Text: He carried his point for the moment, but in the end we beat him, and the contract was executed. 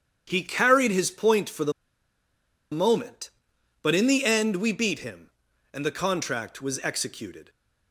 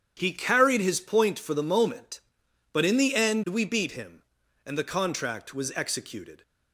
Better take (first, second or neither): second